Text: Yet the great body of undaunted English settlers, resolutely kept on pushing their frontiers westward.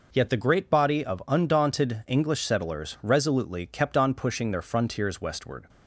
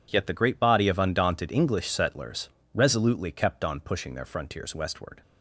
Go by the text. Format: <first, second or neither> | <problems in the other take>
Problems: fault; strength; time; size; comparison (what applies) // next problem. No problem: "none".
neither | none